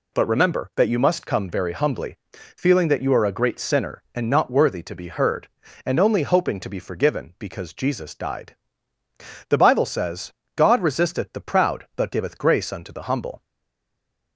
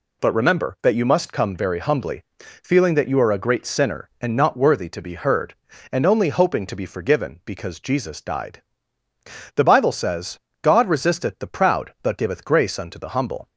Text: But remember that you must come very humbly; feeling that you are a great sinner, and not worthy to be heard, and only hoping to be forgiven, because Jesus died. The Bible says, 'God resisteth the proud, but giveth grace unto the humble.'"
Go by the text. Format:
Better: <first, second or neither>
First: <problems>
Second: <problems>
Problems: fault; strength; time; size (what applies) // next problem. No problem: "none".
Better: second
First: stays silent after the last word; from 13.4 s on; 0.9 s long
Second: none